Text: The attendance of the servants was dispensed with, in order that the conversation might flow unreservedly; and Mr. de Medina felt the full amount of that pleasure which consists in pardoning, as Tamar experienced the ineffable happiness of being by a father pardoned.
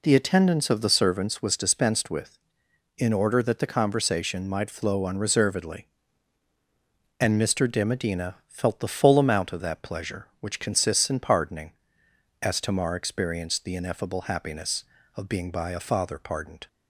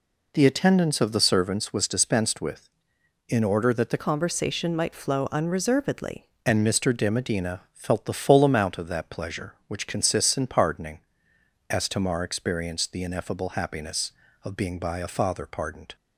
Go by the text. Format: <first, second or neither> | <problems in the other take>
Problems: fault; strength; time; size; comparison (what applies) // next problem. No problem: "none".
first | changes voice from "conversation" to "unreservedly"; from 3.9 to 6.2 s; 2.3 s long